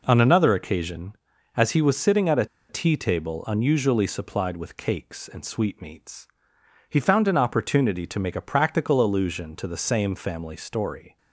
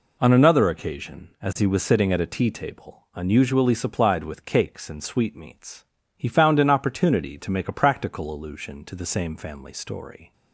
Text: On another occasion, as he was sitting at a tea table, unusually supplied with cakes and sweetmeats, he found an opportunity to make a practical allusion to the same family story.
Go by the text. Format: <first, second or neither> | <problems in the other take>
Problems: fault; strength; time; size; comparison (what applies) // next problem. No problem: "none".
second | pauses between "a" and "tea"; slight; at 2.4 s; 0.23 s long